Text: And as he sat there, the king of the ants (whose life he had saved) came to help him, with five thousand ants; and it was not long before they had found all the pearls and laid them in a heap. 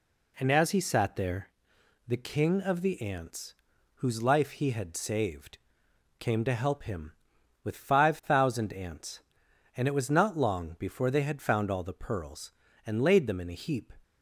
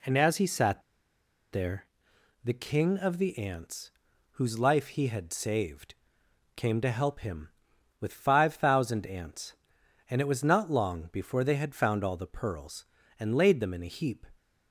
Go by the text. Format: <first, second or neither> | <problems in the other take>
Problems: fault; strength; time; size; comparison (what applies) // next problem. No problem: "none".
first | pauses between "sat" and "there"; noticeable; at 0.8 s; 0.71 s long